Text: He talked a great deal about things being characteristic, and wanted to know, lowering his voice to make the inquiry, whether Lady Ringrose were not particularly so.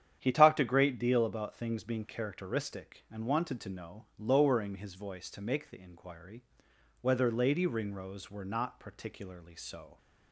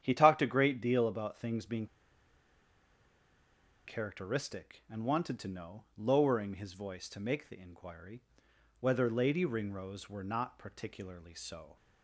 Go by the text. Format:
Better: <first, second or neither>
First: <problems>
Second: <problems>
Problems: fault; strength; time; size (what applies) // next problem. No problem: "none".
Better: first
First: starts louder than the rest; strong; until 1.2 s; 9.5 dB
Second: starts louder than the rest; strong; until 1.0 s; 9.5 dB // pauses between "being" and "characteristic"; strong; at 1.8 s; 2.0 s long